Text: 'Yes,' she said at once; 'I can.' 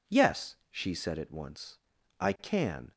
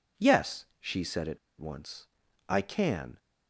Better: first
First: none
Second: pauses between "at" and "once"; slight; at 1.3 s; 0.21 s long

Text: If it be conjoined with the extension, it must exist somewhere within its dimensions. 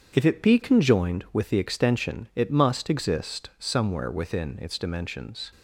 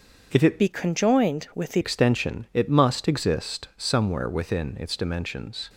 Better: first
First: starts louder than the rest; strong; until 1.1 s; 7.5 dB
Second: starts louder than the rest; until 1.3 s; 6.5 dB // changes voice from "be" to "the"; from 0.5 to 1.8 s; 1.3 s long

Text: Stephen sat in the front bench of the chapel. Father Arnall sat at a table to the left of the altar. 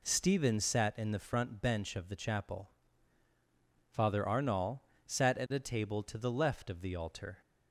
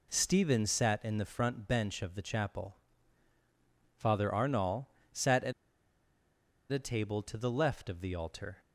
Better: first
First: pauses between "Arnall" and "sat"; slight; at 4.8 s; 0.26 s long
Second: pauses between "Arnall" and "sat"; slight; at 4.8 s; 0.26 s long // pauses between "at" and "a"; at 5.5 s; 1.1 s long

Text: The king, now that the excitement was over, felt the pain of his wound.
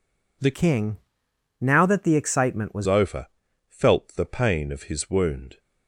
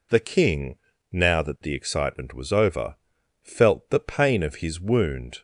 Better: second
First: changes voice from "king" to "was"; from 0.5 to 2.8 s; 2.3 s long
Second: none

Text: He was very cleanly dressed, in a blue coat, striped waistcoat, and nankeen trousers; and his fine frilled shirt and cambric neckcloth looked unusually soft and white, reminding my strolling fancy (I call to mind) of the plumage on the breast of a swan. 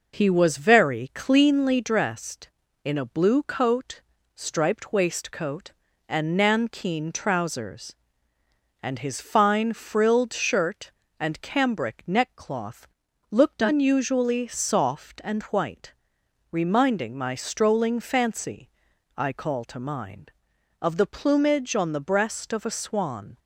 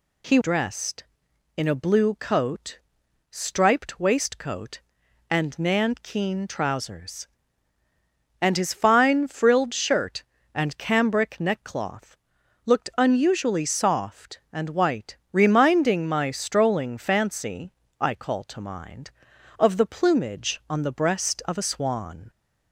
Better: first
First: pauses between "neckcloth" and "looked"; noticeable; at 12.8 s; 0.46 s long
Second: skips "was very cleanly"; at 0.4 s // pauses between "neckcloth" and "looked"; noticeable; at 12.1 s; 0.48 s long

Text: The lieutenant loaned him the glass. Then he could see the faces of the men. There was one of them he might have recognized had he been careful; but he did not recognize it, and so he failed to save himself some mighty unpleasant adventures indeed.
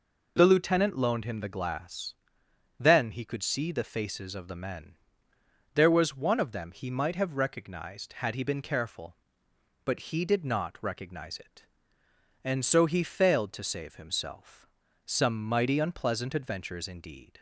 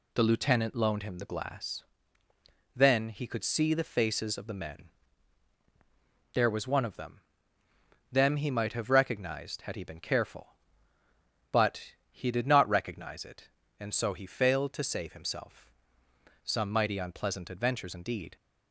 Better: first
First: pauses between "himself" and "some"; at 14.6 s; 0.38 s long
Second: says "them" twice; at 8.1 s // pauses between "but" and "he"; slight; at 11.9 s; 0.18 s long // pauses between "himself" and "some"; noticeable; at 15.6 s; 0.74 s long

